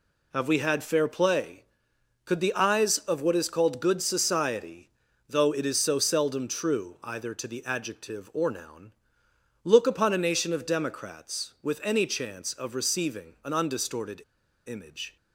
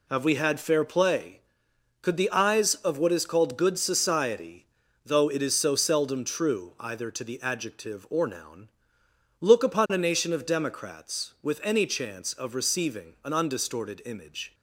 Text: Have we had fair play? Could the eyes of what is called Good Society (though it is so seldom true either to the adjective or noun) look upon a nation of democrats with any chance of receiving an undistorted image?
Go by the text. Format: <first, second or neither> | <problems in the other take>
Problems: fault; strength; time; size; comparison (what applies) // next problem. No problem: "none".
second | pauses between "undistorted" and "image"; at 14.2 s; 0.45 s long